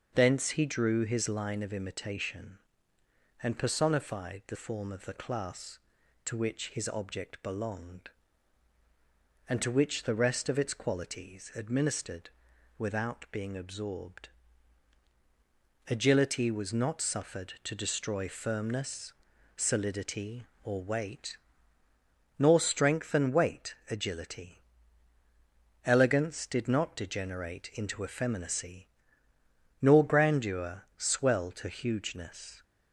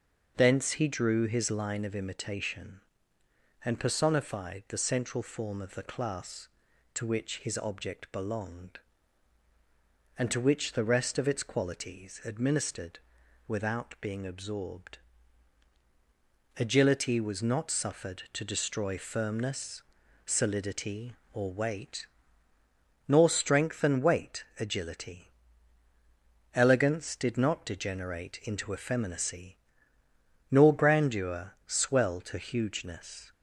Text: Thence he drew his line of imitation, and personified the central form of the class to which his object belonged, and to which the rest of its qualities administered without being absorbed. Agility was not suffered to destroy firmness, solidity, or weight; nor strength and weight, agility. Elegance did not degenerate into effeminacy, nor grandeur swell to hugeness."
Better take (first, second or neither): second